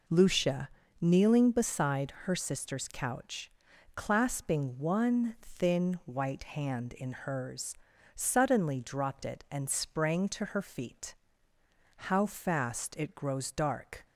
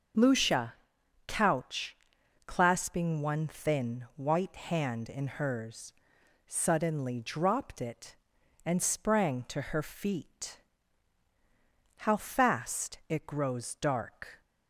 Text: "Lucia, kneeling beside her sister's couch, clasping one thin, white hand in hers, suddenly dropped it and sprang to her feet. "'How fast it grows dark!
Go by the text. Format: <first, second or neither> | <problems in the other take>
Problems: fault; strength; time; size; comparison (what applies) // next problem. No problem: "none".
first | starts louder than the rest; until 1.7 s; 6.5 dB // skips "kneeling beside her sister's"; at 0.9 s